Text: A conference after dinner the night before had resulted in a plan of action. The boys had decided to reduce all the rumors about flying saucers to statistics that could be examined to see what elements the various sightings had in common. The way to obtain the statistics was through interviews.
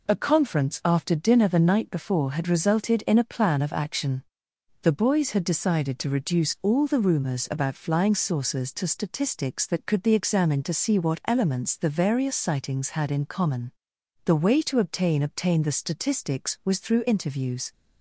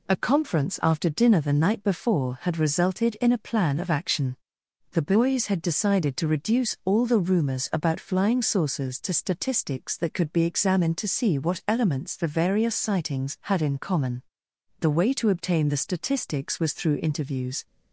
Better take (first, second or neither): second